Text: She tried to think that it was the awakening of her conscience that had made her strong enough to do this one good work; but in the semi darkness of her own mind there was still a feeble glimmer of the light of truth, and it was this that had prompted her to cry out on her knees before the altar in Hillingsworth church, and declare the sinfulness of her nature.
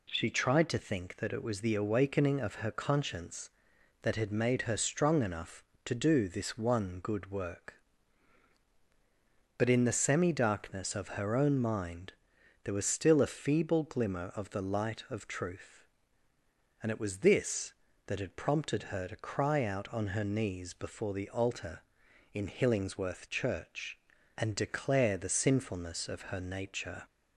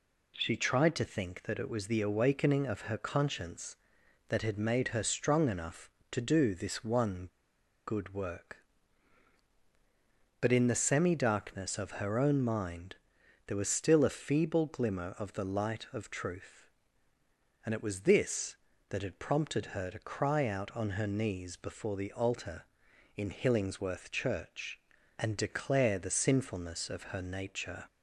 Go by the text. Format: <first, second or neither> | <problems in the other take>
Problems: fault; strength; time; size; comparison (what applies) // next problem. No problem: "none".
first | pauses between "one" and "good"; noticeable; at 7.2 s; 0.61 s long // pauses between "mind" and "there"; noticeable; at 12.9 s; 0.48 s long; noticeable in the first